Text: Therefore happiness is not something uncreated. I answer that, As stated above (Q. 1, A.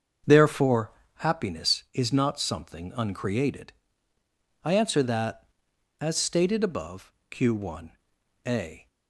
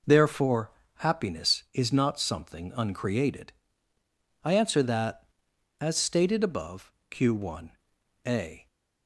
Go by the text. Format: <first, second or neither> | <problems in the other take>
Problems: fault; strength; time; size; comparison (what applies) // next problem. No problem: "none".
second | starts louder than the rest; until 1.2 s; 6.5 dB // pauses between "Therefore" and "happiness"; slight; at 0.9 s; 0.26 s long; slight in the second